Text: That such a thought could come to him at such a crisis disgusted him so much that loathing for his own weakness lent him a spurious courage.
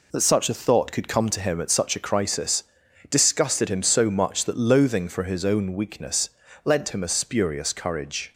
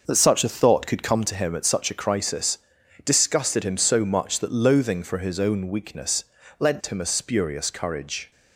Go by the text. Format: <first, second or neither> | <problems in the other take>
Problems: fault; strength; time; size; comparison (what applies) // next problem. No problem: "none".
first | starts louder than the rest; noticeable; until 1.2 s; 5.5 dB // pauses between "crisis" and "disgusted"; noticeable; at 2.5 s; 0.46 s long; noticeable in the first // pauses between "weakness" and "lent"; slight; at 6.2 s; 0.36 s long; slight in the first